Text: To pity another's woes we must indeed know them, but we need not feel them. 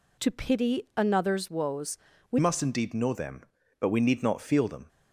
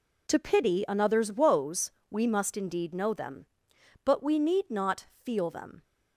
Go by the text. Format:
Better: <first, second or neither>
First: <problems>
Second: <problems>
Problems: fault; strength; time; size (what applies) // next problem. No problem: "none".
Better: second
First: pauses between "woes" and "we"; slight; at 1.9 s; 0.36 s long // changes voice at "must"; from 2.3 s on; 2.5 s long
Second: pauses between "woes" and "we"; slight; at 1.9 s; 0.18 s long